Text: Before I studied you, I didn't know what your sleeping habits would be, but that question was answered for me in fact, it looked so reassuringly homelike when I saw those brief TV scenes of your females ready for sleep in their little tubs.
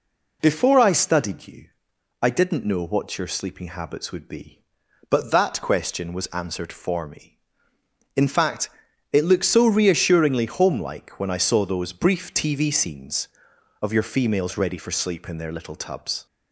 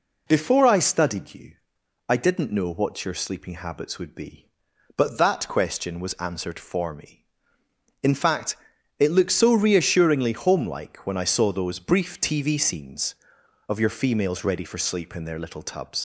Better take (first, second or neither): first